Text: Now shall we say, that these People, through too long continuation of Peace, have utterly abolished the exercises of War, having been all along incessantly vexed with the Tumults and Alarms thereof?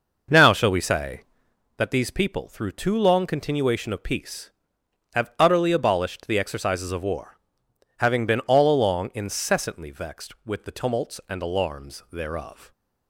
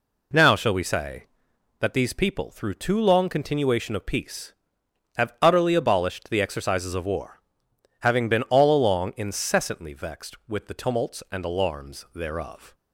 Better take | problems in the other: second | starts louder than the rest; noticeable; until 1.6 s; 6 dB

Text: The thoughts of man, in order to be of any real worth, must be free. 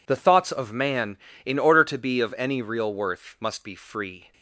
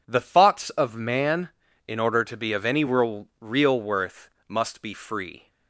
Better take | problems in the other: first | says "real" twice; at 3.3 s

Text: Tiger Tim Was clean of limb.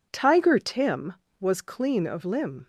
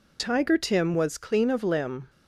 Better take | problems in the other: neither | none

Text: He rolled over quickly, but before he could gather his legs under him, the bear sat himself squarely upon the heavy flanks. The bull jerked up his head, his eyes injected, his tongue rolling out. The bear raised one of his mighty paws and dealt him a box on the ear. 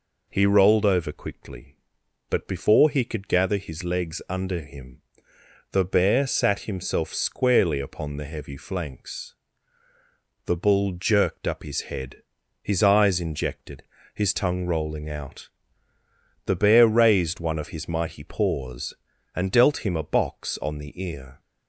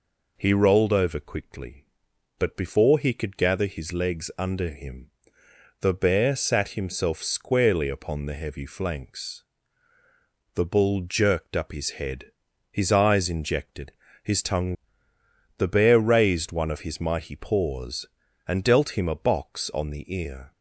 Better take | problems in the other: first | skips "rolling out"; at 15.1 s

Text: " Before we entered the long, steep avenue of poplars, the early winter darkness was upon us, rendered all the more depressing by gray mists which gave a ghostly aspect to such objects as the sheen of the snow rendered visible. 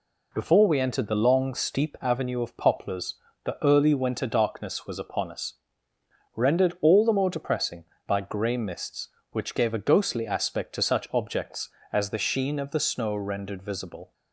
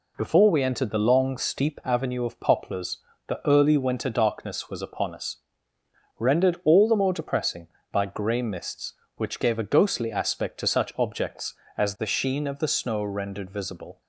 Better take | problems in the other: neither | none

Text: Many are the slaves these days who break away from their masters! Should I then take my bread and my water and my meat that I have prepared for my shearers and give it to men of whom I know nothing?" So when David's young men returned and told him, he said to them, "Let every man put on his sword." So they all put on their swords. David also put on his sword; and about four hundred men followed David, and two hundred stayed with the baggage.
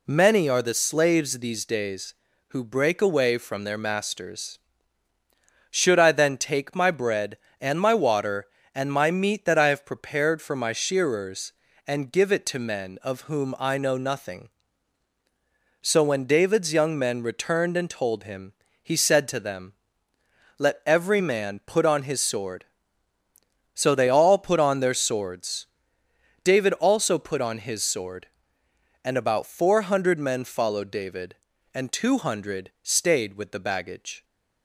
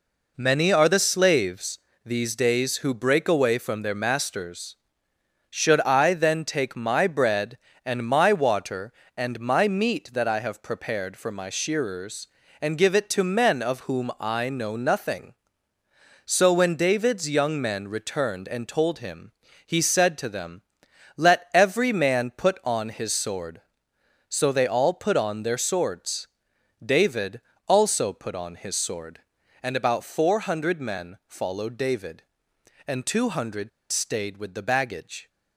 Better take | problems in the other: first | pauses between "slaves" and "these"; slight; at 1.7 s; 0.26 s long // pauses between "David" and "also"; slight; at 27.4 s; 0.28 s long // pauses between "hundred" and "stayed"; slight; at 33.6 s; 0.22 s long

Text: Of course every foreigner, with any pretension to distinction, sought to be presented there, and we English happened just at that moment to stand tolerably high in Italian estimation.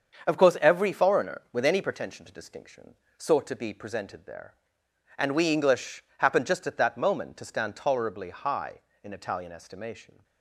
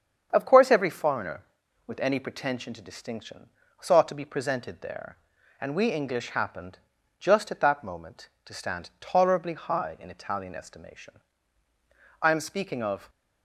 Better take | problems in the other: first | starts louder than the rest; strong; until 1.3 s; 7.5 dB; also in the first // pauses between "happened" and "just"; at 6.7 s; 0.40 s long // goes on to say "I am speaking of"; noticeable; from 12.2 s on; 0.88 s long

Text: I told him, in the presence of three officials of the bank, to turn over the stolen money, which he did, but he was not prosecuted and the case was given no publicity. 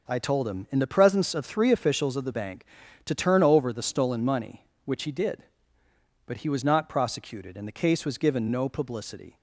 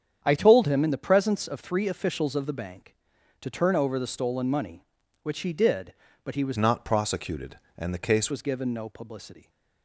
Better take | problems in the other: first | starts louder than the rest; strong; until 1.2 s; 8.5 dB // changes voice from "not" to "case"; from 6.5 to 8.3 s; 1.8 s long

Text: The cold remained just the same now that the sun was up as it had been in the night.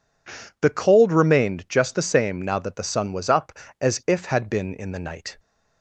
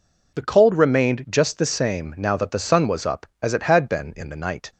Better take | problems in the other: second | says "if" for "it"; at 4.0 s

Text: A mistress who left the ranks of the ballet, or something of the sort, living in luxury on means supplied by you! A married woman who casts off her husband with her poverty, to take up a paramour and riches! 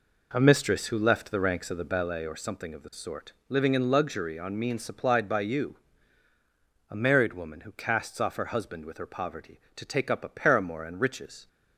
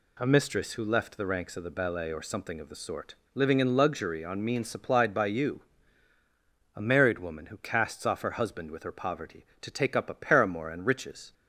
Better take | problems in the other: second | starts louder than the rest; noticeable; until 2.2 s; 4 dB

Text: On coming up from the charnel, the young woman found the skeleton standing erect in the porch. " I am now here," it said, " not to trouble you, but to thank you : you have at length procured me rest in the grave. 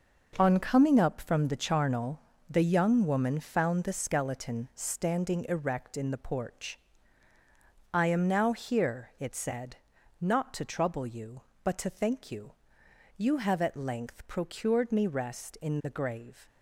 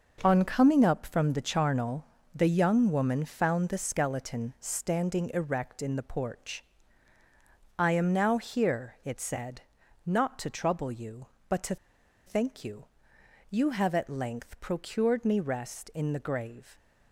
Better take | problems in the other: first | starts louder than the rest; until 1.2 s; 6.5 dB; also in the first // pauses between "to" and "thank"; noticeable; at 11.7 s; 0.50 s long

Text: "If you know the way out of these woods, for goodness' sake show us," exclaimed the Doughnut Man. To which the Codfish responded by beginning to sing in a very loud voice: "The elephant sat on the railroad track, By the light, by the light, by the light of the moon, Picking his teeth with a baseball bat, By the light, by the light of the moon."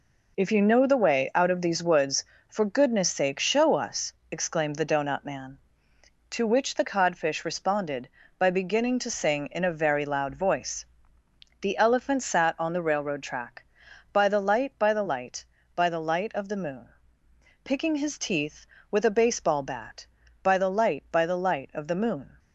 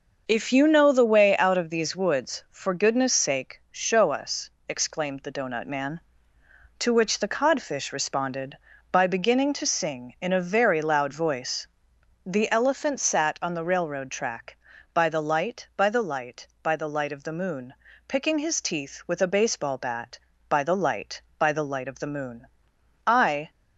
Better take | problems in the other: first | starts louder than the rest; noticeable; until 1.2 s; 6 dB // goes on to say "I"; slight; from 23.0 s on; 0.44 s long

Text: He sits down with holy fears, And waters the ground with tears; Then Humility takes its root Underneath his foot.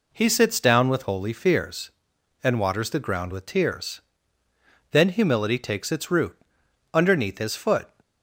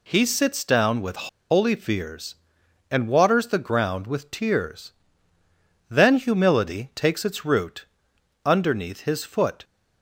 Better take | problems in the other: first | pauses between "with" and "holy"; slight; at 1.2 s; 0.23 s long // pauses between "root" and "Underneath"; noticeable; at 7.8 s; 0.58 s long; noticeable in the first

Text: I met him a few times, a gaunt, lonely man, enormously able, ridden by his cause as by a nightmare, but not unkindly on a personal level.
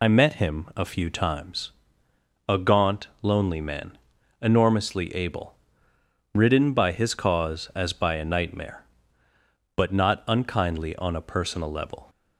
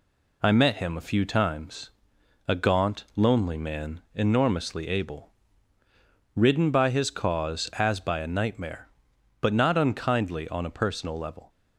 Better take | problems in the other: second | loses the start of "I"; at 0.0 s; 40 ms

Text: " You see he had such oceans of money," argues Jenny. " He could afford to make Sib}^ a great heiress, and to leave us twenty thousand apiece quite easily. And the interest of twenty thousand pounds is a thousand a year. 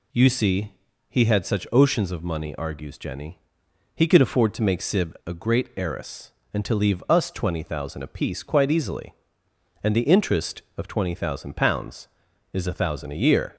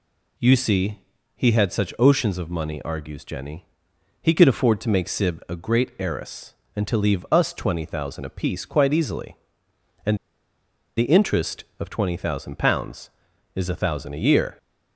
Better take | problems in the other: first | pauses between "see" and "he"; slight; at 0.9 s; 0.36 s long; slight in the first // pauses between "And" and "the"; noticeable; at 10.1 s; 0.81 s long

